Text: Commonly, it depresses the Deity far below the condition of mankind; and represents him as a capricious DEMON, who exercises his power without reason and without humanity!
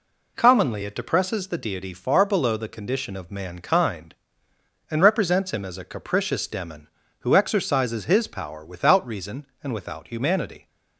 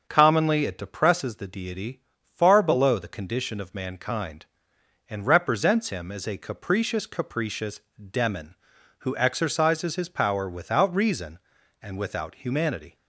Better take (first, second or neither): first